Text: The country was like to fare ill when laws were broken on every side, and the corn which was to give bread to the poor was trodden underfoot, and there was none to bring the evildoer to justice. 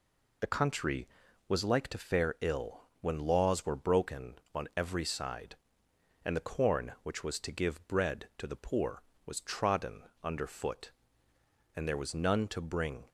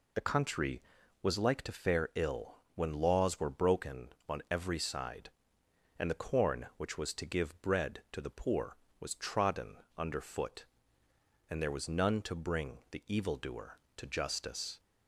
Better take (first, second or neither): second